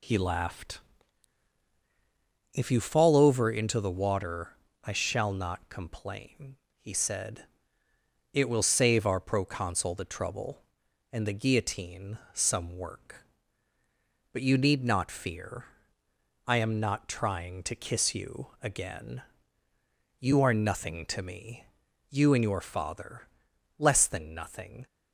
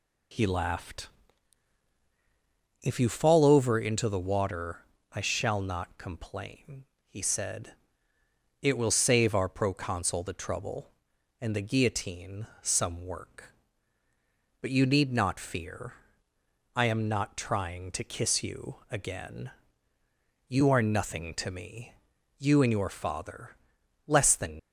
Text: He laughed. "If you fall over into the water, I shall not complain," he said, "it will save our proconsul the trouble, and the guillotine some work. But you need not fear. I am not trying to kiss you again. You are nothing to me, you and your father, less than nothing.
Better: first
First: pauses between "guillotine" and "some"; slight; at 12.1 s; 0.16 s long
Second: pauses between "guillotine" and "some"; slight; at 12.4 s; 0.16 s long // stops before "nothing"; at 24.5 s

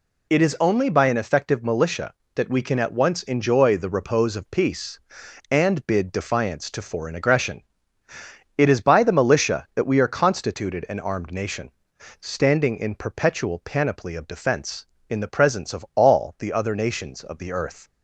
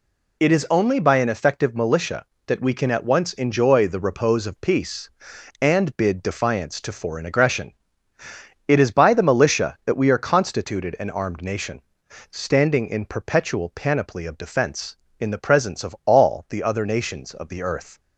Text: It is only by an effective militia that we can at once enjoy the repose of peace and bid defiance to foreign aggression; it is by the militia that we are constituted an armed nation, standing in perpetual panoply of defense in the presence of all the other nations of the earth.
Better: neither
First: none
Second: none

